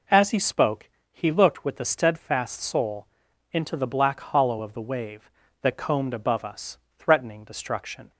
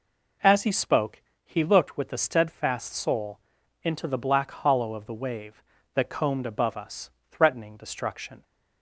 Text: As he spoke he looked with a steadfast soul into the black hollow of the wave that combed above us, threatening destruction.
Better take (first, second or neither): neither